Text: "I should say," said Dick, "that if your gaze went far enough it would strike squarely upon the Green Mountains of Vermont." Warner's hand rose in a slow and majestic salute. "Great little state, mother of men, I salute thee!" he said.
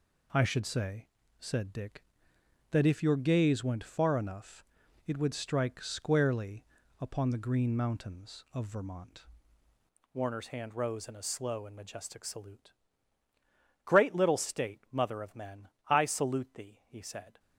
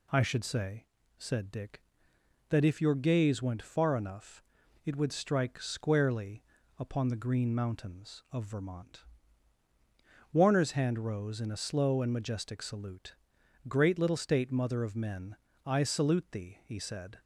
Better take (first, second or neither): second